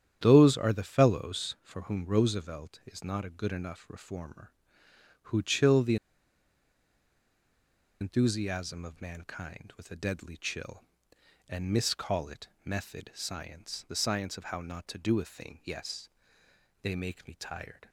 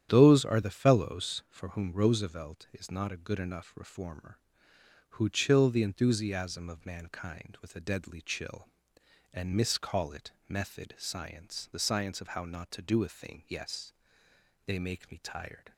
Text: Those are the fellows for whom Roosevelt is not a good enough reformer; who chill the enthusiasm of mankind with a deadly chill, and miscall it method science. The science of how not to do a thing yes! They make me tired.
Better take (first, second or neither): second